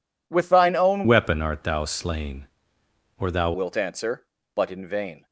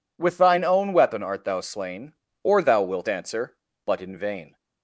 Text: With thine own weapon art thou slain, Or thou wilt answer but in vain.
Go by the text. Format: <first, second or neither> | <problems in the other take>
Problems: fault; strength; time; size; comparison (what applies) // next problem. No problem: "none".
second | changes voice from "weapon" to "thou"; from 1.0 to 3.5 s; 2.5 s long